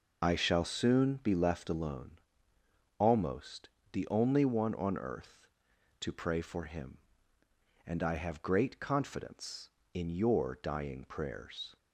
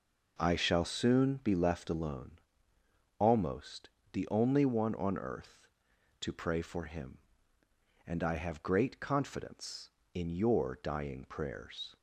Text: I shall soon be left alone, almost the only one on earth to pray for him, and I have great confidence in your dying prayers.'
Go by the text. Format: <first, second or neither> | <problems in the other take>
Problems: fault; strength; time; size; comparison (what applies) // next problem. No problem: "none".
second | loses the start of "I"; at 0.2 s; 40 ms // pauses between "almost" and "the"; slight; at 3.6 s; 0.22 s long; slight in the second